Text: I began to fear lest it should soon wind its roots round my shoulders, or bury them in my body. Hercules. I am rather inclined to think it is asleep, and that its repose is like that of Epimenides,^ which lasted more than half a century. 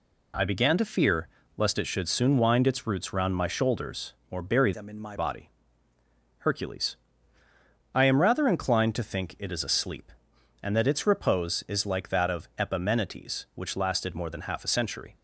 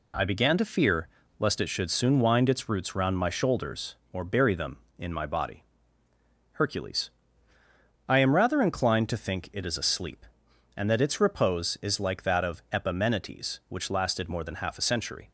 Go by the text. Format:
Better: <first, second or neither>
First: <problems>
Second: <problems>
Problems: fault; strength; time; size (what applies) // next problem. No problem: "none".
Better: second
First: pauses between "fear" and "lest"; slight; at 1.2 s; 0.28 s long // changes voice from "them" to "my"; from 4.7 to 5.1 s; 0.4 s long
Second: pauses between "fear" and "lest"; slight; at 1.0 s; 0.30 s long